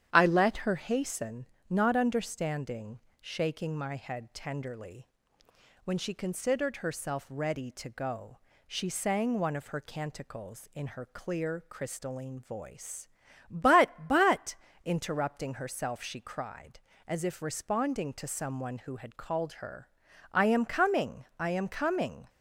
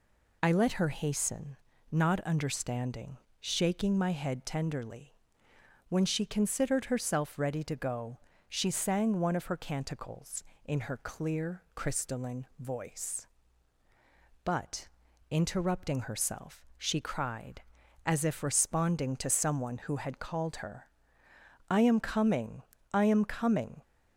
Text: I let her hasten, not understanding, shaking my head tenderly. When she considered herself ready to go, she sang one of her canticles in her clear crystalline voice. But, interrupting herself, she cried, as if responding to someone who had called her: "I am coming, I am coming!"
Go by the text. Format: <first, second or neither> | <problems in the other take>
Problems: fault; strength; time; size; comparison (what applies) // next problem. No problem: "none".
second | starts louder than the rest; strong; until 1.1 s; 10 dB // says "But" twice; at 14.0 s